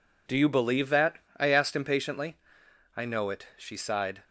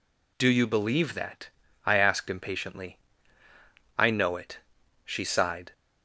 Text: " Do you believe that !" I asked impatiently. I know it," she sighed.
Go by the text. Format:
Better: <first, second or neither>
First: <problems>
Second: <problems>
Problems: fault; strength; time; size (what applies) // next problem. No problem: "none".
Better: neither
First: none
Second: none